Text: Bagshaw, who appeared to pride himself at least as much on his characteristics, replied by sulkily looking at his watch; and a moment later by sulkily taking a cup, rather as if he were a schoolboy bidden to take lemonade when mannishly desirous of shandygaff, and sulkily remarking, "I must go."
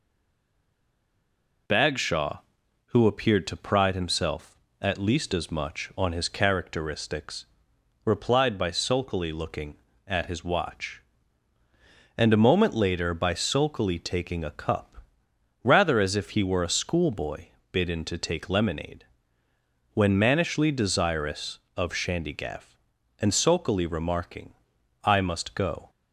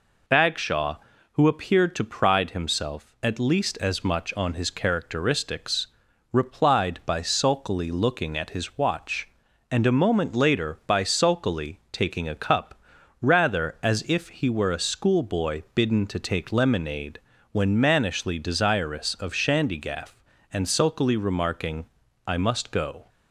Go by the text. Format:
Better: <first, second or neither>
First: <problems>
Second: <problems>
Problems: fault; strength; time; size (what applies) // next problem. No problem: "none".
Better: second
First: stays silent before the first word; noticeable; until 1.6 s; 1.6 s long // pauses between "schoolboy" and "bidden"; slight; at 17.4 s; 0.26 s long // pauses between "lemonade" and "when"; noticeable; at 19.0 s; 0.90 s long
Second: pauses between "lemonade" and "when"; slight; at 17.1 s; 0.34 s long